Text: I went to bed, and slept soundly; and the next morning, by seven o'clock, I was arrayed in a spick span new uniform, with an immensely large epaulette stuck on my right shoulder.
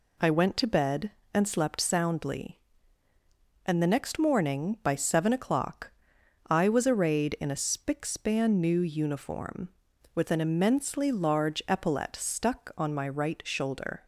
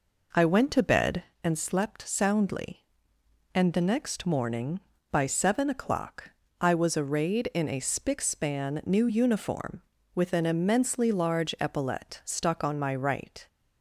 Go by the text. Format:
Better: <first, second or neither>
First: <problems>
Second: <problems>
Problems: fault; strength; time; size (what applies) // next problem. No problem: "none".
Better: first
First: none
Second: stops before "shoulder"; at 13.4 s